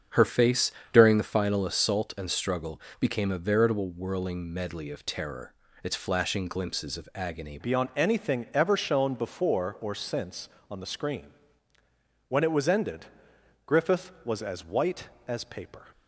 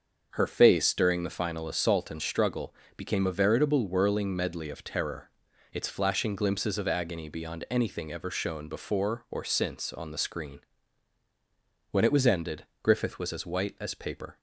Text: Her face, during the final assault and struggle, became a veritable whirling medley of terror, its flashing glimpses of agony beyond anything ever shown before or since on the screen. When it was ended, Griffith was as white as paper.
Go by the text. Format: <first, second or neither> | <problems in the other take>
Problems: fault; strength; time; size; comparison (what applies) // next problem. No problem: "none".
second | starts louder than the rest; strong; until 1.3 s; 7 dB; also in the second // changes voice at "beyond"; from 7.5 s on; 8.3 s long